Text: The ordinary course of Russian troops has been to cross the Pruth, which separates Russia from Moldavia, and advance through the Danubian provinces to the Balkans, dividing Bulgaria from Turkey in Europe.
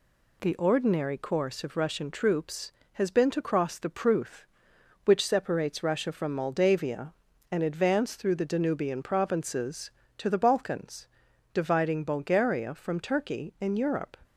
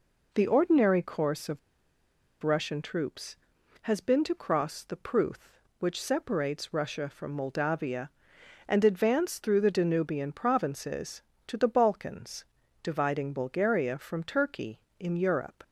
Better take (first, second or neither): first